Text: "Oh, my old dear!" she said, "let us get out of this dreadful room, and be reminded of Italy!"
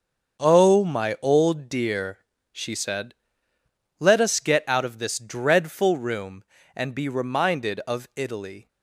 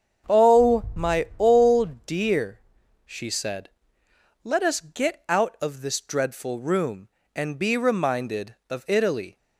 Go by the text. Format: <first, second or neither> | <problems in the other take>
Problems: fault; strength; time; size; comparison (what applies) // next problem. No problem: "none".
neither | starts louder than the rest; the same in both